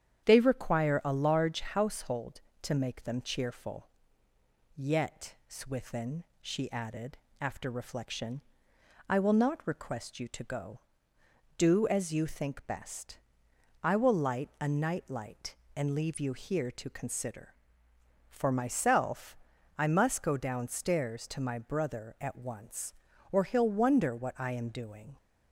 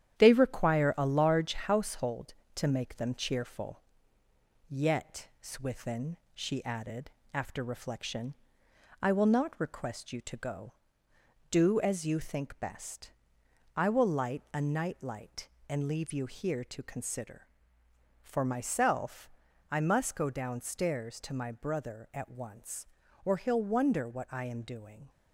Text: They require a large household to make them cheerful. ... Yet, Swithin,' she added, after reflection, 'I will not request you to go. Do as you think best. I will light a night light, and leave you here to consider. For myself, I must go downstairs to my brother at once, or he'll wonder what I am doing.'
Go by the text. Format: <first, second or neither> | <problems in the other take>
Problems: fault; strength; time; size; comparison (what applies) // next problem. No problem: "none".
first | gets quieter; noticeable; throughout; 4.5 dB // starts louder than the rest; strong; until 1.2 s; 10 dB; strong in the first